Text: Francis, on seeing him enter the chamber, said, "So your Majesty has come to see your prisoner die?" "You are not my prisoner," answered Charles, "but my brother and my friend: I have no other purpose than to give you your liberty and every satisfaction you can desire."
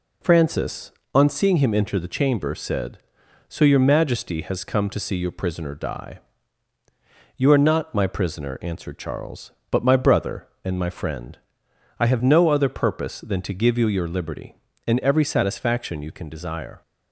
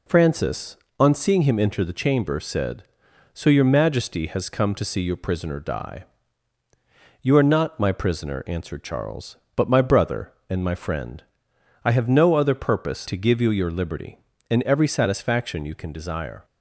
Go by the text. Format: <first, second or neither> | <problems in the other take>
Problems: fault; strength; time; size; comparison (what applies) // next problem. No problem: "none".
first | skips "than"; at 13.0 s